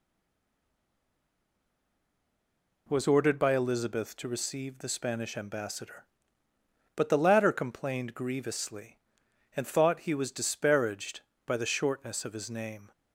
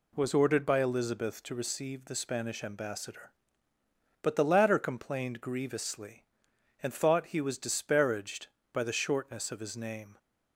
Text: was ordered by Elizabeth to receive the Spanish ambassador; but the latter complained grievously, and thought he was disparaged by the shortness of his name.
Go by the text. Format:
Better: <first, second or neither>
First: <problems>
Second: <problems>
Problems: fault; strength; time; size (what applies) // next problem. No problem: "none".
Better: second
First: stays silent before the first word; strong; until 2.8 s; 2.8 s long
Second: none